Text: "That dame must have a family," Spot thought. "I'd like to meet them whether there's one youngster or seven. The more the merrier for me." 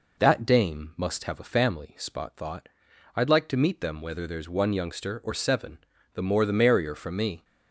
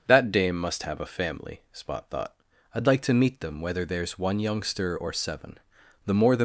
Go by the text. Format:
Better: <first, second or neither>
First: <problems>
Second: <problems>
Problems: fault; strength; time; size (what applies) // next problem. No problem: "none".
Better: first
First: none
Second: starts louder than the rest; noticeable; until 1.0 s; 6 dB // stops before "merrier for me"; at 6.3 s